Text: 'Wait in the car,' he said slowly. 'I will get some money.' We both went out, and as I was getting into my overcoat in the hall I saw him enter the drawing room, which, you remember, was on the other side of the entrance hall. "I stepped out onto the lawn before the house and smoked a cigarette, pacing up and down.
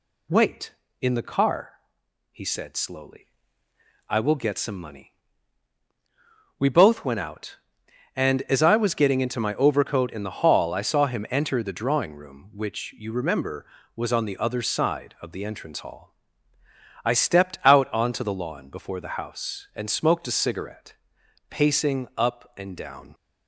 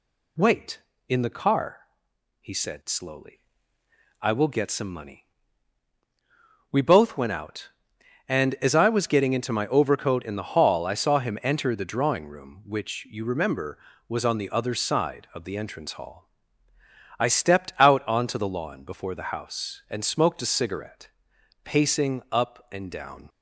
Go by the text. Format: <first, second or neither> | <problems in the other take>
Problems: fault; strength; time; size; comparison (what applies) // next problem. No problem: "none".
neither | none